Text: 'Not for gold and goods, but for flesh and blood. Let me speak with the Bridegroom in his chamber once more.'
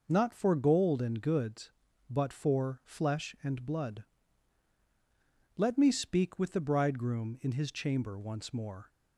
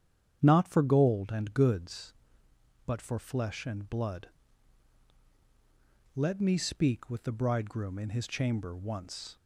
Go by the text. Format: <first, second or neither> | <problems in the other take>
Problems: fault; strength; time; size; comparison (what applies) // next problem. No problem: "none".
first | starts louder than the rest; strong; until 1.4 s; 9 dB // stops before "more"; at 9.3 s